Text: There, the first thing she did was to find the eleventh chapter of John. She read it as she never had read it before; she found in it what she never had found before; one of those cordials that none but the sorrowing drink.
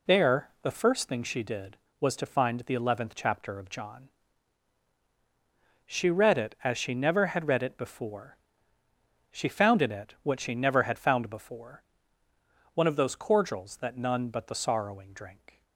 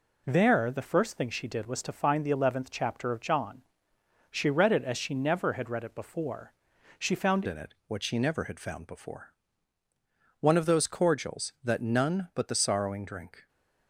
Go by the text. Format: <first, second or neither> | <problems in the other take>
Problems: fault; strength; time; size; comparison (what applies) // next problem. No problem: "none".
first | changes voice at "in"; from 7.4 s on; 6.0 s long